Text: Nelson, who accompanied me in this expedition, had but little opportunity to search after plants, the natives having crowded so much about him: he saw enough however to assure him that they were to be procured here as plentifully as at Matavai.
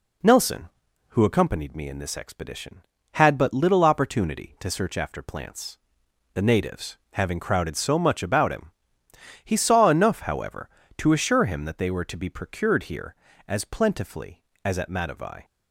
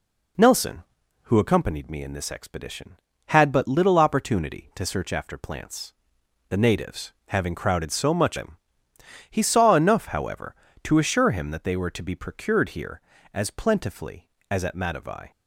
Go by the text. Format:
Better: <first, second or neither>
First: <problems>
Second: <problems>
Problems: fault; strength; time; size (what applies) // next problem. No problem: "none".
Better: first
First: none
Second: skips "about"; at 8.3 s